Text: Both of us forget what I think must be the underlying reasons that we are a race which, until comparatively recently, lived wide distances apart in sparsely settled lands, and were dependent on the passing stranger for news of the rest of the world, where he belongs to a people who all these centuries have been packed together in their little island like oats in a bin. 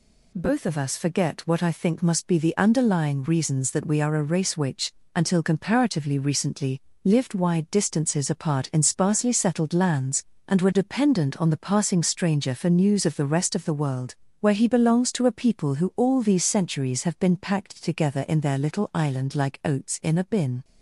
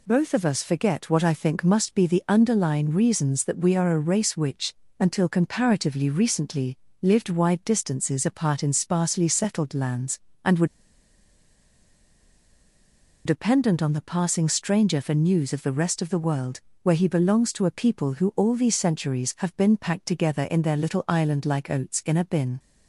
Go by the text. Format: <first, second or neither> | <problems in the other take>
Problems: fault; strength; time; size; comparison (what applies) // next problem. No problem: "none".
first | pauses between "were" and "dependent"; strong; at 10.6 s; 2.6 s long